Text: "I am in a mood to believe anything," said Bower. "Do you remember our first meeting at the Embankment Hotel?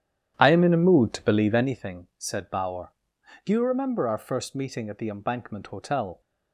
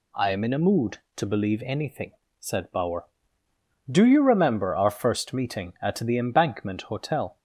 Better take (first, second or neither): second